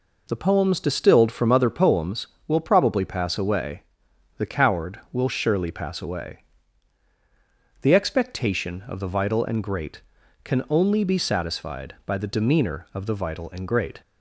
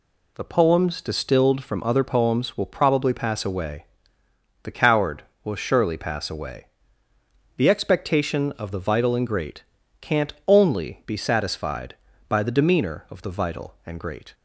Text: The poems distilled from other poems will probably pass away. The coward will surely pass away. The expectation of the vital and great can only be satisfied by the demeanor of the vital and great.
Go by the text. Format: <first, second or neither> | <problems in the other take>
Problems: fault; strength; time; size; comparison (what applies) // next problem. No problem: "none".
first | says "can't" for "can"; at 9.9 s